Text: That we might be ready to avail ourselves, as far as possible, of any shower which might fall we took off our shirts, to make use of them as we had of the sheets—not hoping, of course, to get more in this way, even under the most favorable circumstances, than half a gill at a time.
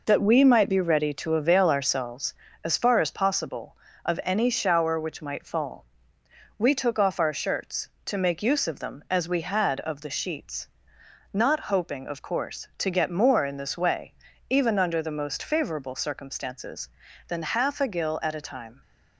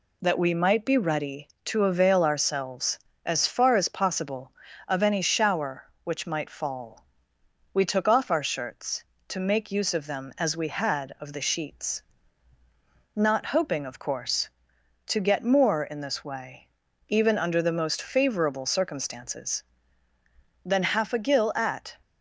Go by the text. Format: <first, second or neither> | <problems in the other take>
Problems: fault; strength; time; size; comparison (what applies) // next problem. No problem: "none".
first | pauses between "fall" and "we"; noticeable; at 7.0 s; 0.66 s long; noticeable in the first // stops before "a time"; at 22.0 s